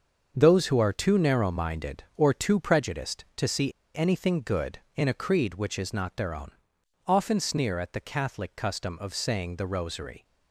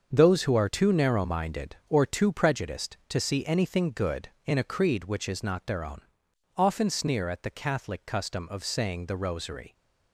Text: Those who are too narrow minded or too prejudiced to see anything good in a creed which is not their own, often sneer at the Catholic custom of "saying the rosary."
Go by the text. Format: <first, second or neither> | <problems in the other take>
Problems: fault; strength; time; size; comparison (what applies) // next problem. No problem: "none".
second | starts louder than the rest; until 1.3 s; 6.5 dB; also in the second // pauses between "see" and "anything"; slight; at 3.7 s; 0.24 s long